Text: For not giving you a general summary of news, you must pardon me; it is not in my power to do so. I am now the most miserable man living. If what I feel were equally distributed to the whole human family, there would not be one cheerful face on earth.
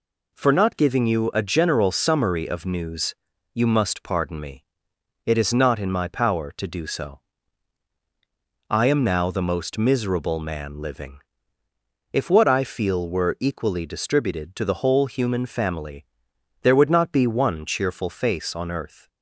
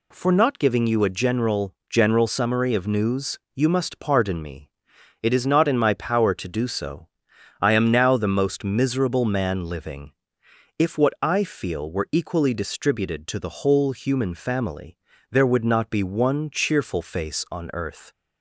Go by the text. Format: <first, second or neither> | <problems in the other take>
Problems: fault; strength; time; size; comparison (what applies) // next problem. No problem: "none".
first | says "general" twice; at 1.8 s